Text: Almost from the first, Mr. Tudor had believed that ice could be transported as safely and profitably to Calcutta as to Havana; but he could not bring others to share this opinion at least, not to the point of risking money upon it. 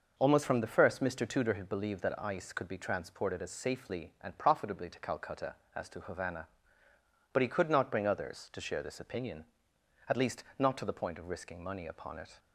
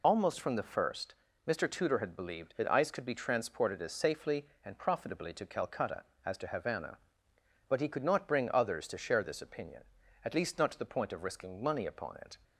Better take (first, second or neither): first